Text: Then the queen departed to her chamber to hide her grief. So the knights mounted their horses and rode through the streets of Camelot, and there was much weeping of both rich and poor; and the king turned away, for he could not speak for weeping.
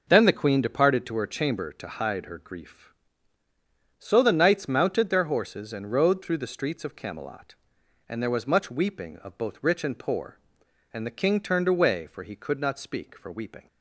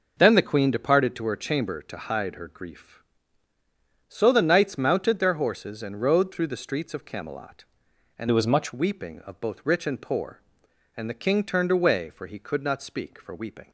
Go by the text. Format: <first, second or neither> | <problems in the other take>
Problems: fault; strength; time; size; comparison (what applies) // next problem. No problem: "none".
first | changes voice from "there" to "much"; from 8.2 to 8.7 s; 0.5 s long